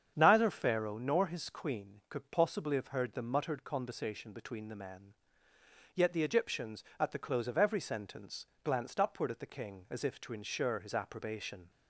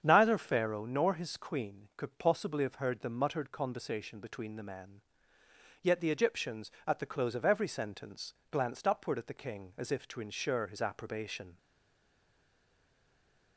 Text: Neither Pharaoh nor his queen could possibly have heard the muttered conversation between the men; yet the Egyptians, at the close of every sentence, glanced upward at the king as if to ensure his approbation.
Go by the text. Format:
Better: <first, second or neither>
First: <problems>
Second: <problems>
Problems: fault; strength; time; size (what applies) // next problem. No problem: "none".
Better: first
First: starts louder than the rest; strong; until 1.1 s; 7.5 dB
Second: starts louder than the rest; strong; until 1.0 s; 7.5 dB // stays silent after the last word; noticeable; from 11.5 s on; 2.0 s long